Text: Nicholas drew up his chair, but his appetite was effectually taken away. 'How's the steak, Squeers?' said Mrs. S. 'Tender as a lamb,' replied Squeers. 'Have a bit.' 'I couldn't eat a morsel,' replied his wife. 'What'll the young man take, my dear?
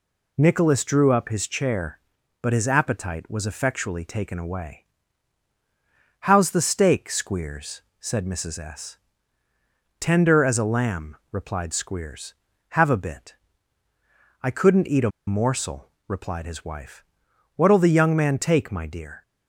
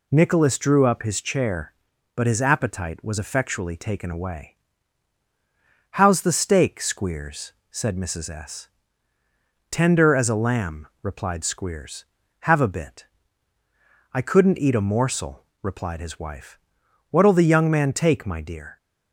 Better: second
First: pauses between "a" and "morsel"; slight; at 15.0 s; 0.17 s long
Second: none

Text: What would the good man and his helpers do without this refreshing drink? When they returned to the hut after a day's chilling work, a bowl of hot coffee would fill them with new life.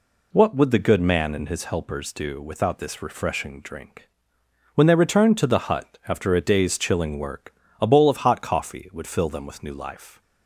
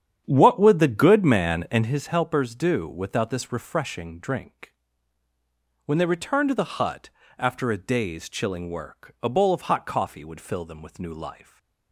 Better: first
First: none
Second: starts louder than the rest; strong; until 1.9 s; 9 dB // pauses between "hut" and "after"; slight; at 7.0 s; 0.30 s long

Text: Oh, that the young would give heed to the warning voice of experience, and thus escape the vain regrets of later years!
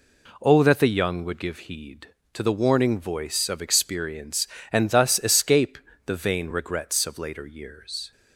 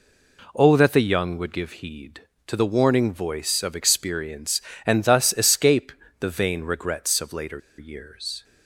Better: first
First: pauses between "escape" and "the"; slight; at 5.7 s; 0.28 s long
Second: pauses between "escape" and "the"; slight; at 5.9 s; 0.28 s long // pauses between "later" and "years"; slight; at 7.6 s; 0.19 s long

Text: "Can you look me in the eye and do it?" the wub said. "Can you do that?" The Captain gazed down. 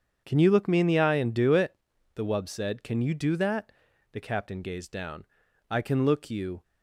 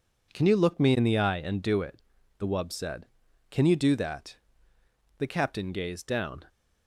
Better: second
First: starts louder than the rest; strong; until 1.2 s; 7.5 dB // goes on to say "I can look you"; noticeable; from 5.7 s on; 0.92 s long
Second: none

